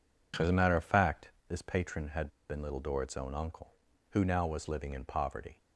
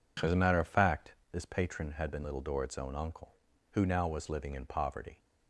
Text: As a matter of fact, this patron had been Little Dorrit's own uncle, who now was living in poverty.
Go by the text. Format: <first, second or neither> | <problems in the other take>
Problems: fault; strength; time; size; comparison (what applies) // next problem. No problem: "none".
second | pauses between "had" and "been"; slight; at 2.2 s; 0.20 s long